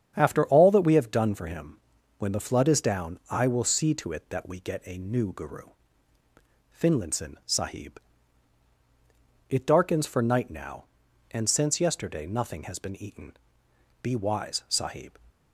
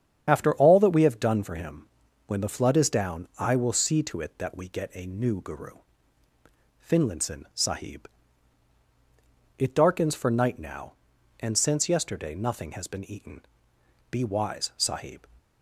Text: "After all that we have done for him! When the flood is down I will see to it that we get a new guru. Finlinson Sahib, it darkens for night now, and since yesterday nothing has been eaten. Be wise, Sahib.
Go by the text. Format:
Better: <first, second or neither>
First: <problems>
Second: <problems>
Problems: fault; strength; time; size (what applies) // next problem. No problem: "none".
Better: first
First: starts louder than the rest; strong; until 1.1 s; 8.5 dB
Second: loses the start of "After"; at 0.2 s; 40 ms // starts louder than the rest; strong; until 1.3 s; 8.5 dB